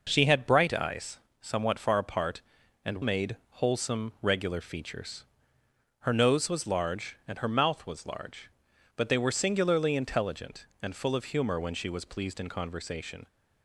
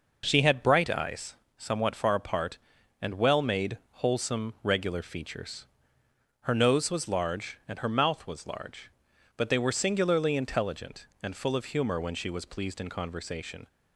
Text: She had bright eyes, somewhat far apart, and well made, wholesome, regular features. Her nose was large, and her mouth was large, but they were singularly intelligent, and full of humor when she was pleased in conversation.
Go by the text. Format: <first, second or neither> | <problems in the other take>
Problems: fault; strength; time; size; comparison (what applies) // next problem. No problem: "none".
second | skips "well"; at 3.0 s